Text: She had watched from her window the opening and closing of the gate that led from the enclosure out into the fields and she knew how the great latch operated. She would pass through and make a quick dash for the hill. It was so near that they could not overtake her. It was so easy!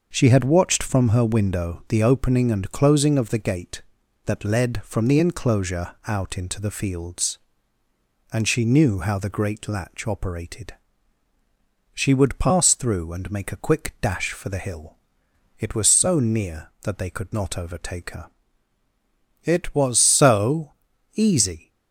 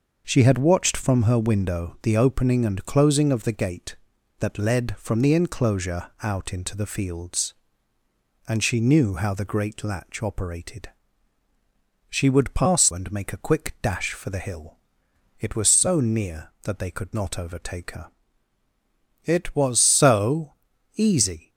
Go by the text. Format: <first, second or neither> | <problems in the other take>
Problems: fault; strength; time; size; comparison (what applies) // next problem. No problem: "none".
first | skips "through"; at 12.9 s // pauses between "so" and "easy"; at 20.5 s; 0.42 s long; also in the first